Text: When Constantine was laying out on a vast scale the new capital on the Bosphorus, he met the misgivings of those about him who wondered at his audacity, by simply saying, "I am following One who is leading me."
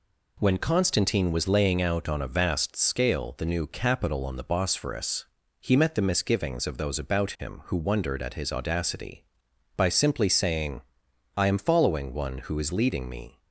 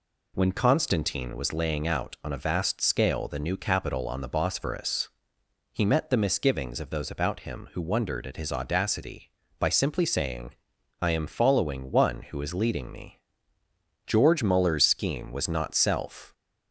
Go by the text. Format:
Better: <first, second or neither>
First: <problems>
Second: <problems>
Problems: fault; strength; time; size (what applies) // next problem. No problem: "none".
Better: first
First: none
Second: goes on to say "George Muller's scheme was not self"; strong; from 14.0 s on; 2.2 s long